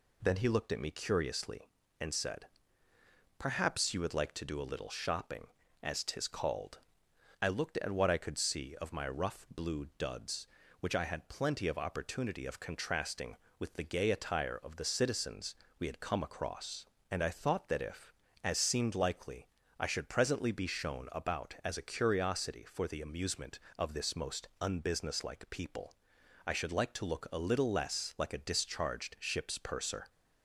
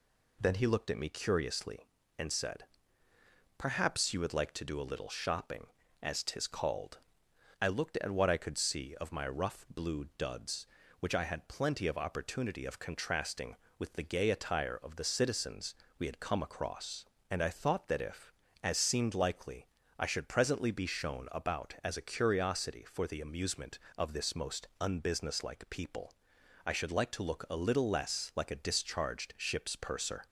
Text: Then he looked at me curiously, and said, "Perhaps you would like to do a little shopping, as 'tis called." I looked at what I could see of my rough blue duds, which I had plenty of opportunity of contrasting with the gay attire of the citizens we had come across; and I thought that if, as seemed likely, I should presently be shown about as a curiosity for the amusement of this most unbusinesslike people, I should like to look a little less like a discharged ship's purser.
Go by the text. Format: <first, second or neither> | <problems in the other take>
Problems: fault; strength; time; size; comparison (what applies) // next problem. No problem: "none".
neither | pauses between "citizens" and "we"; slight; the same in both